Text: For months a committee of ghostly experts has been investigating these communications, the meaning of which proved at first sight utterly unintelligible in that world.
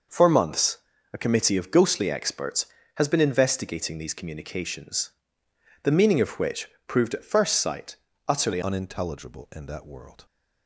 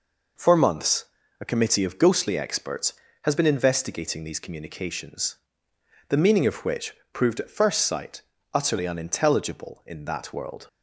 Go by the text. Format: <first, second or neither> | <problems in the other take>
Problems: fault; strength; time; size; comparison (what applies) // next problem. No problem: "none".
second | pauses between "months" and "a"; slight; at 0.7 s; 0.36 s long; slight in the second // pauses between "which" and "proved"; slight; at 6.6 s; 0.20 s long; slight in the second // pauses between "sight" and "utterly"; slight; at 7.9 s; 0.32 s long; slight in the second // changes voice at "unintelligible"; from 8.6 s on; 1.6 s long